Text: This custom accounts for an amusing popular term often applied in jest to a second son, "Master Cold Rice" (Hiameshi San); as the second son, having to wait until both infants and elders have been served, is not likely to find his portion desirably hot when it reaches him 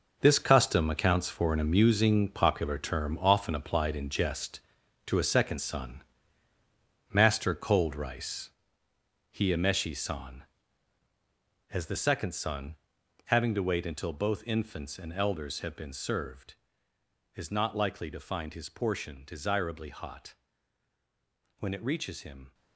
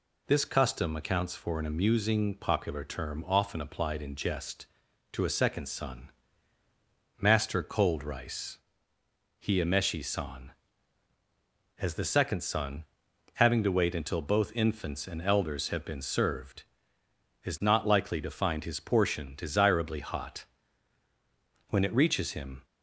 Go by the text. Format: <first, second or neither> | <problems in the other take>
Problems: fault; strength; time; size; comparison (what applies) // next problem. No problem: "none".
second | gets quieter; strong; throughout; 11 dB // pauses between "hot" and "when"; at 20.3 s; 1.2 s long; also in the second